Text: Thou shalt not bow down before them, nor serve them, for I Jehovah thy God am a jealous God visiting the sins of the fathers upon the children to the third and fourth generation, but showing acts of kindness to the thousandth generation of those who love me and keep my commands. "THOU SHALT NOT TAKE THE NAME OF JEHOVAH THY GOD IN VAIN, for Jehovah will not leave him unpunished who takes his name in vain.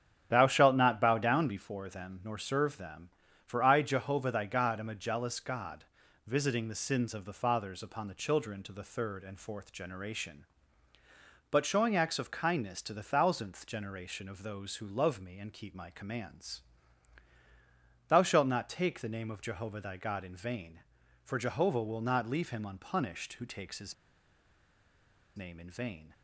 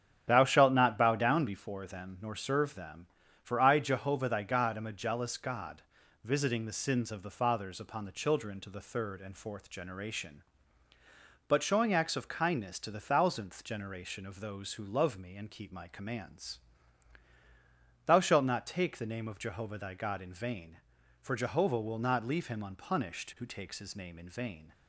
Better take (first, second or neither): second